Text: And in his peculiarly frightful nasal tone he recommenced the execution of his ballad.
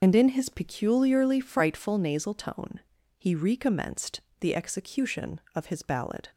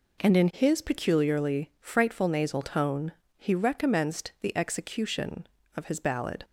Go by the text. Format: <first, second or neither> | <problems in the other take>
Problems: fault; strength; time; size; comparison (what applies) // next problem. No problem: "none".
second | loses the start of "And"; at 0.0 s; 65 ms // pauses between "tone" and "he"; slight; at 2.8 s; 0.36 s long; slight in the second // pauses between "recommenced" and "the"; slight; at 4.2 s; 0.20 s long